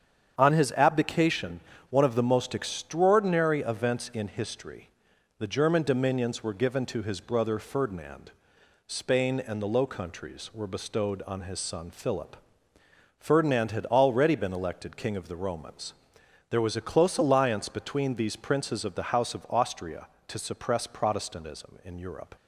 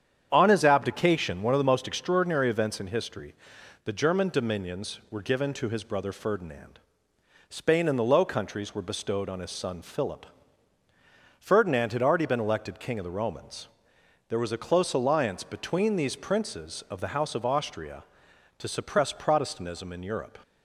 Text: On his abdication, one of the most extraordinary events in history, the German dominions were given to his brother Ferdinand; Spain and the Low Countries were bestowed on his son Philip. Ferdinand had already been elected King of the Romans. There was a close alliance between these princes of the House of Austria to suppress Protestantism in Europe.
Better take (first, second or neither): neither